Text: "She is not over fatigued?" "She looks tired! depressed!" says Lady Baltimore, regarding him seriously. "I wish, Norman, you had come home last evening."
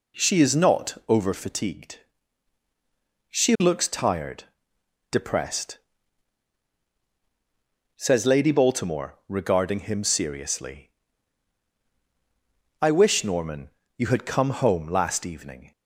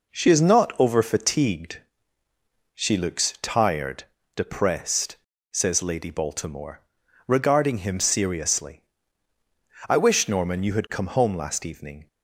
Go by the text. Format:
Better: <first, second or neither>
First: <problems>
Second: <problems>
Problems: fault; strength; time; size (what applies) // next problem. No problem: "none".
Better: neither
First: none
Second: none